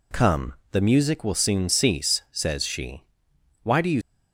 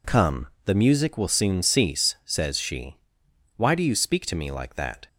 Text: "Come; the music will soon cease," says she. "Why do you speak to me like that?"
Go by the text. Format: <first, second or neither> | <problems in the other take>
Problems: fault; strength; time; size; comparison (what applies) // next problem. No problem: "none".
second | stops before "speak to me like that"; at 4.0 s